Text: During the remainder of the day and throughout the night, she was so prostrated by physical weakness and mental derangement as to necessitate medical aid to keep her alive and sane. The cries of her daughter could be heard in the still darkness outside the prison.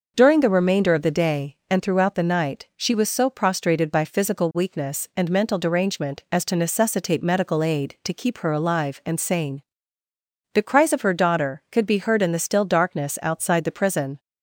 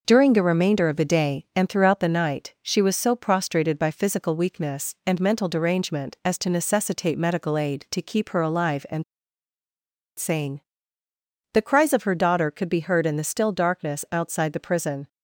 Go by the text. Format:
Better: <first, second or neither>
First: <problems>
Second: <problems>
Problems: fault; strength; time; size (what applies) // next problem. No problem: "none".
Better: first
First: none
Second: pauses between "and" and "sane"; at 9.0 s; 1.1 s long